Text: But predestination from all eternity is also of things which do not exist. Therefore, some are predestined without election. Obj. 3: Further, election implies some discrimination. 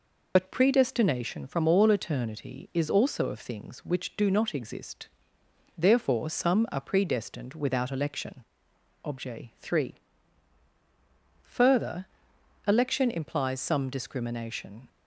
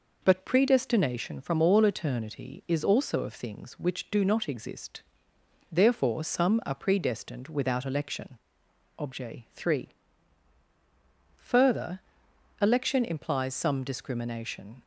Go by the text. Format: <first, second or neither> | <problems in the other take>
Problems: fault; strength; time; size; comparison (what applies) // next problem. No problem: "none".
second | loses the start of "But"; at 0.3 s; 50 ms